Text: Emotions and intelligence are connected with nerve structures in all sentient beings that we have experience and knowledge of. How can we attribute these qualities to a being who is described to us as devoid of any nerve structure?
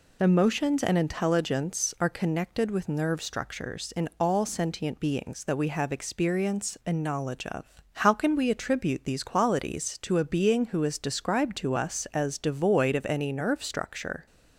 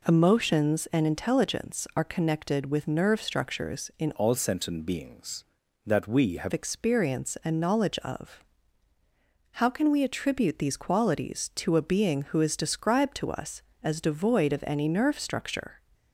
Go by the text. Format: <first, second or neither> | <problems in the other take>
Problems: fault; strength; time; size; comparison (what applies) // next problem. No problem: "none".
first | changes voice from "all" to "have"; from 4.1 to 6.5 s; 2.4 s long